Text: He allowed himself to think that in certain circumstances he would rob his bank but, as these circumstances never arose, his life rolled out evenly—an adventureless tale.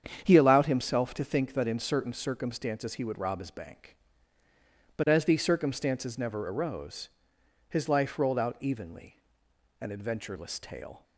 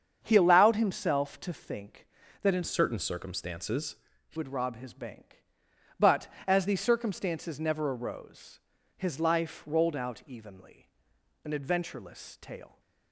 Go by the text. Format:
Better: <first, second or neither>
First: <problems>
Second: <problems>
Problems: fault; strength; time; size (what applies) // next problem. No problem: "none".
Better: first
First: starts louder than the rest; strong; until 1.2 s; 8 dB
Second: starts louder than the rest; strong; until 1.2 s; 7.5 dB // changes voice from "certain" to "he"; from 2.6 to 4.3 s; 1.7 s long // pauses between "circumstances" and "he"; slight; at 3.9 s; 0.34 s long